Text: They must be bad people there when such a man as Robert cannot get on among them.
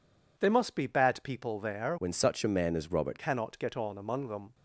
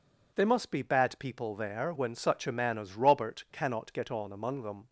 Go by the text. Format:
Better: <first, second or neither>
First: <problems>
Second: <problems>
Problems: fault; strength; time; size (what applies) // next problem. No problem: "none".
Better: second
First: changes voice from "when" to "Robert"; from 1.9 to 3.1 s; 1.2 s long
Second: none